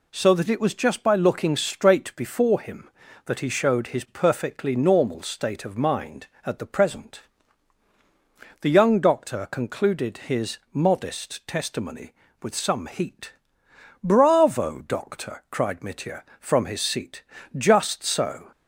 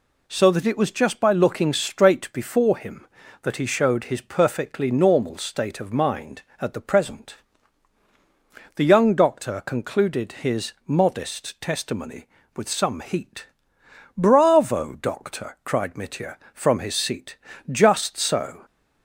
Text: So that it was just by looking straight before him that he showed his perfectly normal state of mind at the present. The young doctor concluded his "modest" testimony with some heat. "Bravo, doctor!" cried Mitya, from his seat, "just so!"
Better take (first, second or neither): neither